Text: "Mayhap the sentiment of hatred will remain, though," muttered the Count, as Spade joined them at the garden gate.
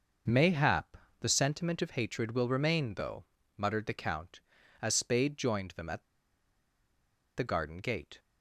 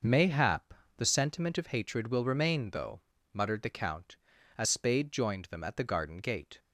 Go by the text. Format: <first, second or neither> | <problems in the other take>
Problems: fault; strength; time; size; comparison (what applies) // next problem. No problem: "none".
second | pauses between "Mayhap" and "the"; slight; at 0.9 s; 0.24 s long; slight in the second // pauses between "at" and "the"; strong; at 6.0 s; 1.3 s long